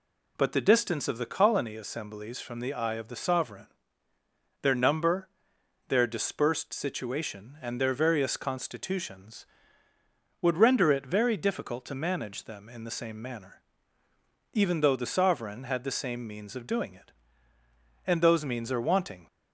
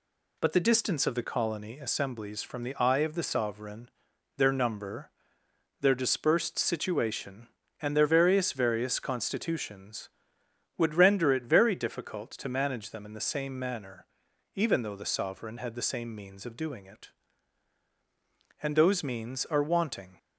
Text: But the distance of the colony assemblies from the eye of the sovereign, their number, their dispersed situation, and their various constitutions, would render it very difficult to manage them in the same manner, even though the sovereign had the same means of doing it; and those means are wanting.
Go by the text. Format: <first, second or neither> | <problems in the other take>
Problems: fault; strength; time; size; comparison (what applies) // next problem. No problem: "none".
first | says "various" twice; at 8.5 s